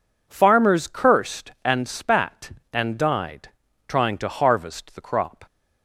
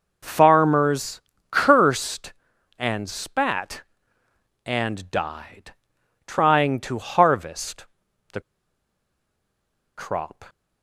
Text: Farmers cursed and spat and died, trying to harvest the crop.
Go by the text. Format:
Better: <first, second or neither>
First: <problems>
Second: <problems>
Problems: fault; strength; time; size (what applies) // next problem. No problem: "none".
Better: first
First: none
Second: pauses between "Farmers" and "cursed"; slight; at 1.1 s; 0.30 s long // pauses between "harvest" and "the"; noticeable; at 7.8 s; 0.46 s long // pauses between "the" and "crop"; strong; at 8.3 s; 1.5 s long